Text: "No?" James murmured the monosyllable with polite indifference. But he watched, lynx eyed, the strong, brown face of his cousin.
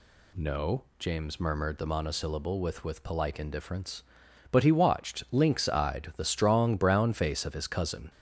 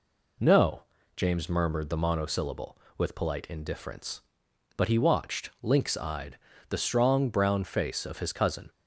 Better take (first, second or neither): second